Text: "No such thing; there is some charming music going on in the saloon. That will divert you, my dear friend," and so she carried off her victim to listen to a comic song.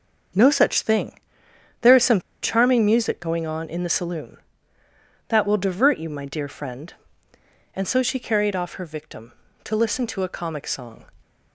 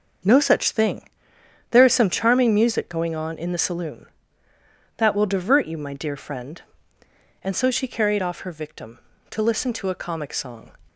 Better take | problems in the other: second | starts louder than the rest; until 1.9 s; 6.5 dB; also in the second // pauses between "some" and "charming"; slight; at 2.1 s; 0.23 s long

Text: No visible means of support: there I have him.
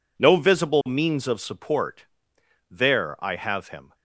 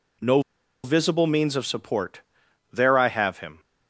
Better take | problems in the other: first | pauses between "No" and "visible"; at 0.4 s; 0.43 s long

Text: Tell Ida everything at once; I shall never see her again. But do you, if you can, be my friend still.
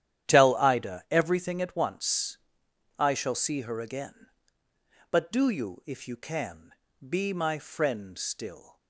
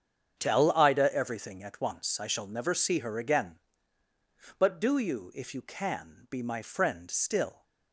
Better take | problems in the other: second | starts louder than the rest; strong; until 1.3 s; 11 dB; strong in the second // skips "never"; at 3.3 s

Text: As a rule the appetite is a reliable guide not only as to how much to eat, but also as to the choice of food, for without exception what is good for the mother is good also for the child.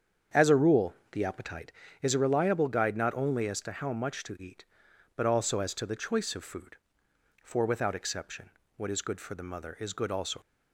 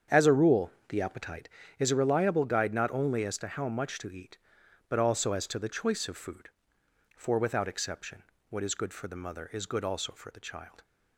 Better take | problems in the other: second | starts louder than the rest; strong; until 1.5 s; 7.5 dB; strong in the second // pauses between "rule" and "the"; slight; at 0.9 s; 0.16 s long; slight in the second // pauses between "exception" and "what"; slight; at 8.4 s; 0.26 s long; slight in the second // stops before "for the child"; at 10.4 s

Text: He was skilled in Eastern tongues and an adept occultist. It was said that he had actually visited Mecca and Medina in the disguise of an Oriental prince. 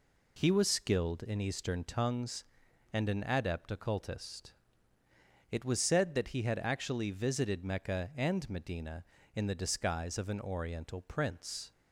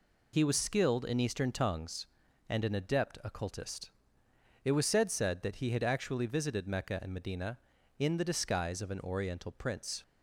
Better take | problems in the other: first | says "said" twice; at 5.1 s

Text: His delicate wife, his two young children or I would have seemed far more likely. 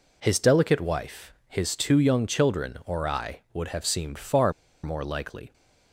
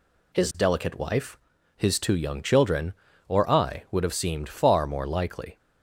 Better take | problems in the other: second | pauses between "far" and "more"; slight; at 4.5 s; 0.31 s long

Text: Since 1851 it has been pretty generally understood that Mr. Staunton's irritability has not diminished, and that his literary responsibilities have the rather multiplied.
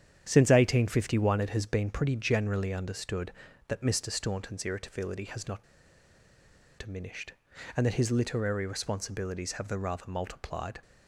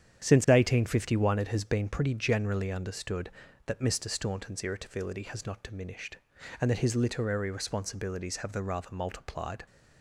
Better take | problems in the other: second | starts louder than the rest; strong; until 1.2 s; 9 dB; strong in the second // pauses between "not" and "diminished"; at 5.6 s; 1.1 s long

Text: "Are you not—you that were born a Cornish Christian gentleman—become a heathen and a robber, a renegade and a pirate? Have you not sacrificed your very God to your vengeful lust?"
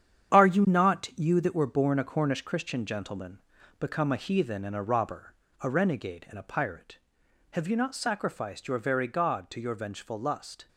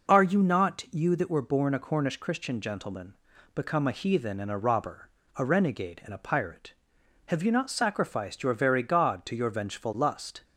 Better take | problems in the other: second | gets quieter; strong; throughout; 9 dB

